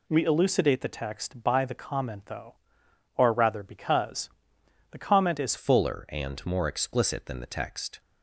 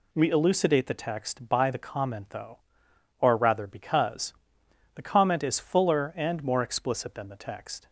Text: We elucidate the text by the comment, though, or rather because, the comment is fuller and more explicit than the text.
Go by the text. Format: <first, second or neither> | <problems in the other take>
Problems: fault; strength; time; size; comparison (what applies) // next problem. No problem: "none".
second | changes voice at "fuller"; from 5.5 s on; 2.4 s long